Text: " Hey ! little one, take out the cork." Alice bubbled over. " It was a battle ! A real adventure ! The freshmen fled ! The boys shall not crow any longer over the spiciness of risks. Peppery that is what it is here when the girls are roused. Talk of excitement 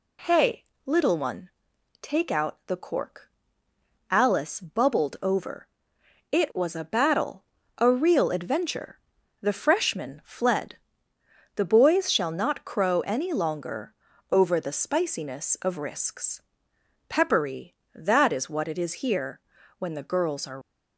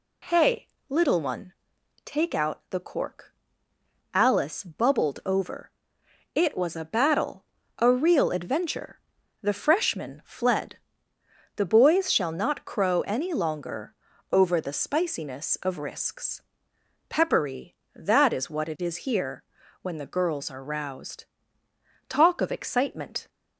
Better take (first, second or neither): second